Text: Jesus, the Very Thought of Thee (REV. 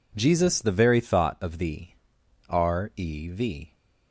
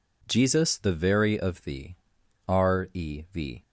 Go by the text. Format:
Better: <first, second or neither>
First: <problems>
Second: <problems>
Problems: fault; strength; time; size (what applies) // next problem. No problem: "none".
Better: first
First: none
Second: skips "Thought"; at 1.3 s